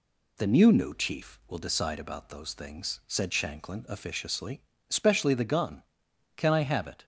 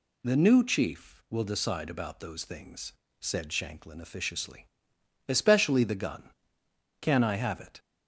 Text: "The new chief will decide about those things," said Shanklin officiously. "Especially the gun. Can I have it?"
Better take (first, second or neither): second